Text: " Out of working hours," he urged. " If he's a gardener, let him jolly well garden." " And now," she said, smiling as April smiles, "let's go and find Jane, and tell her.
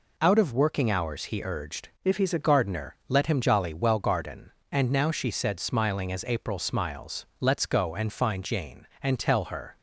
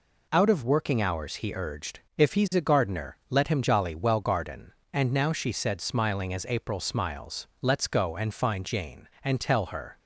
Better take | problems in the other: second | changes voice from "If" to "a"; from 2.0 to 2.4 s; 0.4 s long

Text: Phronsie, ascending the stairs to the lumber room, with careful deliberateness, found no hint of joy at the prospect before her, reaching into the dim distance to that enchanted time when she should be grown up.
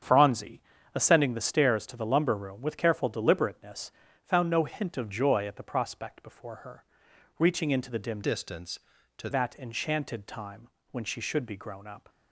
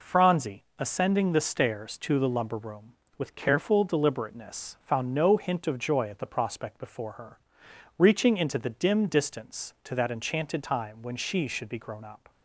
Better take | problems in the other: second | starts louder than the rest; strong; until 1.3 s; 8 dB // changes voice from "distance" to "to"; from 8.2 to 9.2 s; 1.0 s long // pauses between "time" and "when"; slight; at 10.6 s; 0.24 s long

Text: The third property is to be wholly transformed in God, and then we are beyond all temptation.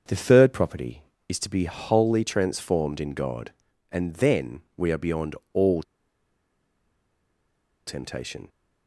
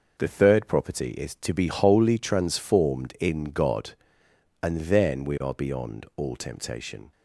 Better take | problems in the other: second | starts louder than the rest; until 1.3 s; 6.5 dB // pauses between "then" and "we"; slight; at 4.6 s; 0.16 s long // pauses between "beyond" and "all"; slight; at 5.3 s; 0.18 s long // pauses between "all" and "temptation"; strong; at 5.8 s; 2.0 s long

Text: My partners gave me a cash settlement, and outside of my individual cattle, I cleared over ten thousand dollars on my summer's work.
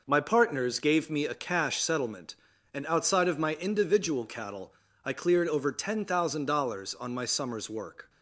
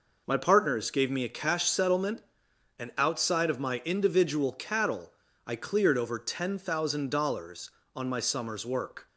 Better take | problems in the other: neither | none

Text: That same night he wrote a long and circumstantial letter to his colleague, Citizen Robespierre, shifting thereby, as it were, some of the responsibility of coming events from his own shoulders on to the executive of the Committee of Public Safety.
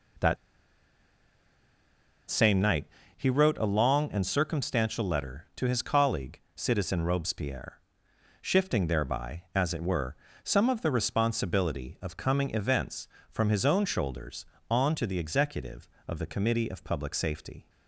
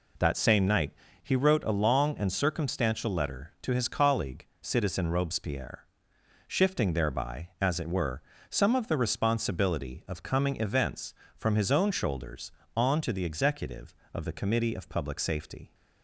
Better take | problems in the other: second | pauses between "That" and "same"; strong; at 0.3 s; 1.9 s long // pauses between "night" and "he"; slight; at 2.8 s; 0.28 s long; slight in the second

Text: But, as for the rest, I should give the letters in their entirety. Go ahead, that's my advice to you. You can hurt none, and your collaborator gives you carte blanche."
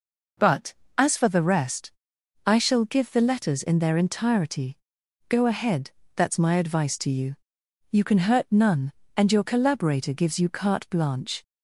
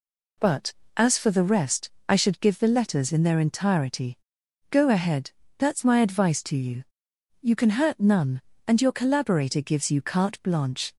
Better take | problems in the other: second | says "shall" for "should"; at 2.5 s

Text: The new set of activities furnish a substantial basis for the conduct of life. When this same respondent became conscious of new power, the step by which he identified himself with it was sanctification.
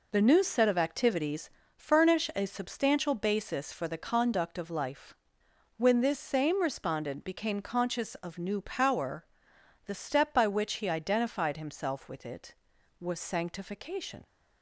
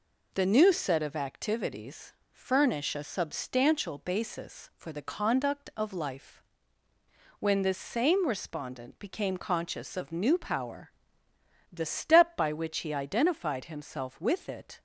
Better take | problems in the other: first | pauses between "activities" and "furnish"; slight; at 2.1 s; 0.18 s long; slight in the first // stops before "was sanctification"; at 14.7 s

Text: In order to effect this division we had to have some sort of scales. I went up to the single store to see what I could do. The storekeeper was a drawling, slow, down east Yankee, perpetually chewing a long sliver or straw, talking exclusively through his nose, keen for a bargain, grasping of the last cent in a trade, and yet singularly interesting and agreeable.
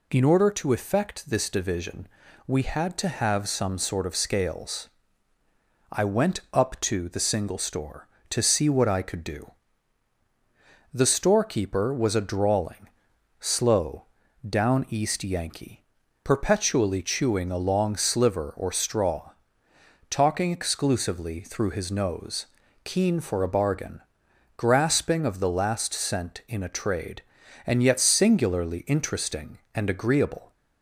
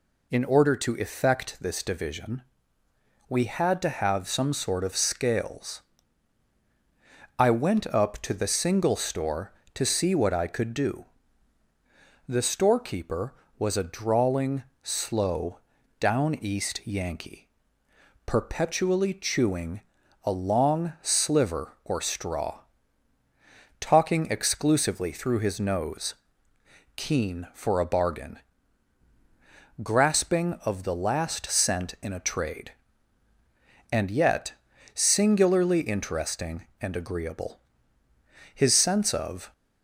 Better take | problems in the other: first | pauses between "division" and "we"; noticeable; at 2.4 s; 0.86 s long; also in the first // pauses between "chewing" and "a"; at 19.7 s; 0.42 s long // pauses between "yet" and "singularly"; at 34.5 s; 0.44 s long // goes on to say "His sense of"; noticeable; from 38.5 s on; 1.0 s long

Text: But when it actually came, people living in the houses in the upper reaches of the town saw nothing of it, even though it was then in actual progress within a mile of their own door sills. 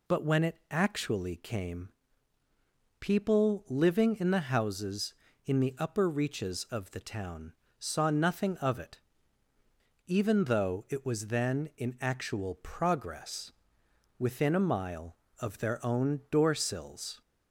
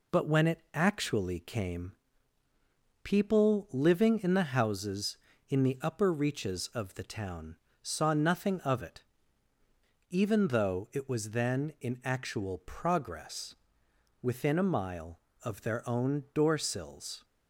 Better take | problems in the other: first | gets quieter; slight; throughout; 3 dB // pauses between "town" and "saw"; slight; at 7.5 s; 0.26 s long; slight in the first // pauses between "progress" and "within"; noticeable; at 13.5 s; 0.68 s long; noticeable in the first

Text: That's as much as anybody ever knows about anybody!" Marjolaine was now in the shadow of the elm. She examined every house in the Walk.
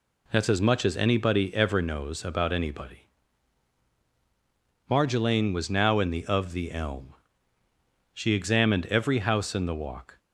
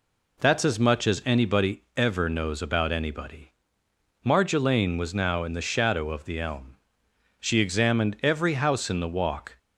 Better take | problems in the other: second | skips "shadow"; at 6.2 s

